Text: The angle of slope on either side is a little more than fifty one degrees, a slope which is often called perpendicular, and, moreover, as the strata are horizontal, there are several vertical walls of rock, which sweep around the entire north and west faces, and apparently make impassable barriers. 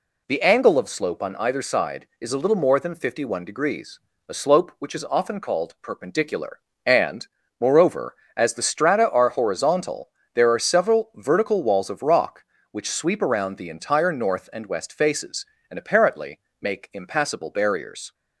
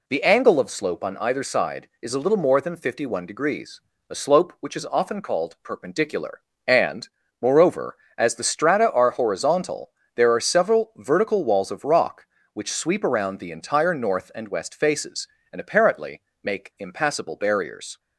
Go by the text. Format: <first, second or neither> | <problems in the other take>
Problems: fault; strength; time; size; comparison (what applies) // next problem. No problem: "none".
neither | pauses between "apparently" and "make"; slight; the same in both